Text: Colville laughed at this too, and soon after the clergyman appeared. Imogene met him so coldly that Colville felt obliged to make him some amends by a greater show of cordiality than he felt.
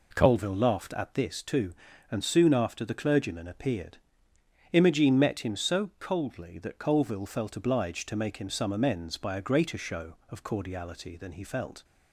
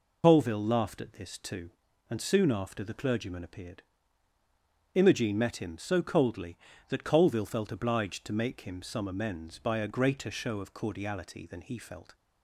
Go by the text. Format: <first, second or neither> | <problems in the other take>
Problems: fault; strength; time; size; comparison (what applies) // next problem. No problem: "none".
first | loses the start of "Colville"; at 0.2 s; 75 ms